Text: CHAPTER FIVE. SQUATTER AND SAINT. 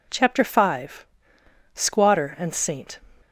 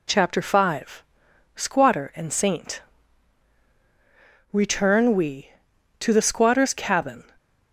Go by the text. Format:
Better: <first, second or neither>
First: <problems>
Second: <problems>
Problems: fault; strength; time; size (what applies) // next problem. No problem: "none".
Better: first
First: none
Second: goes on to say "Return we to the squatter's cabin"; strong; from 4.5 s on; 2.7 s long